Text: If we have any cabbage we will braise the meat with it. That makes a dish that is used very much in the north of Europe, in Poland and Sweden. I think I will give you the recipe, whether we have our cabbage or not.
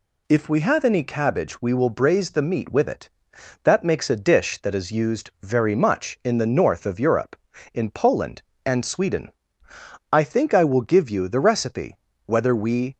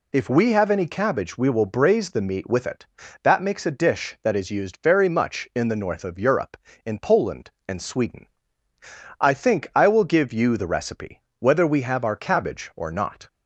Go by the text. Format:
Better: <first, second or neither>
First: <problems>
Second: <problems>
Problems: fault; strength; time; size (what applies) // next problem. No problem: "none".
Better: second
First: stops before "have our cabbage or not"; at 12.9 s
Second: none